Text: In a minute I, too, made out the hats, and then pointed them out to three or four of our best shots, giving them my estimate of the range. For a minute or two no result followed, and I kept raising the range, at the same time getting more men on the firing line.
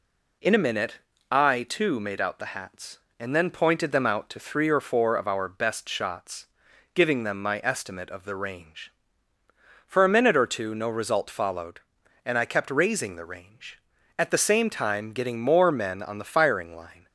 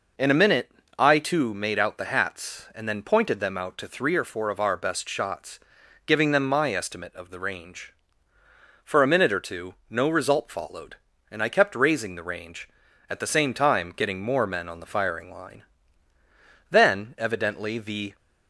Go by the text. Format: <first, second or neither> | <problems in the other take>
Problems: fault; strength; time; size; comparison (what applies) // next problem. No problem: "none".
first | pauses between "minute" and "I"; slight; at 0.6 s; 0.28 s long; slight in the first // pauses between "two" and "no"; slight; at 9.7 s; 0.16 s long // goes on to say "Then evidently the"; from 16.6 s on; 1.4 s long